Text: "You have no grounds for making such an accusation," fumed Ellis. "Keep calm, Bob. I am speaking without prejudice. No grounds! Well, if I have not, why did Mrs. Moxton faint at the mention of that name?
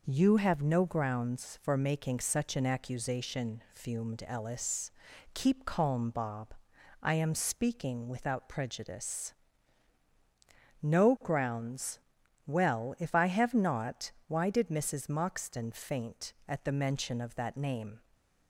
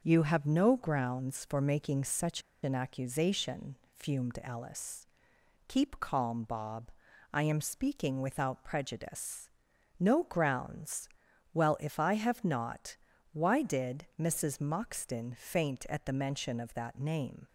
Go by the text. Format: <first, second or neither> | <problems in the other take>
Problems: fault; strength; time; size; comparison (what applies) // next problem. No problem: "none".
first | starts louder than the rest; until 1.0 s; 6.5 dB // pauses between "such" and "an"; slight; at 2.4 s; 0.21 s long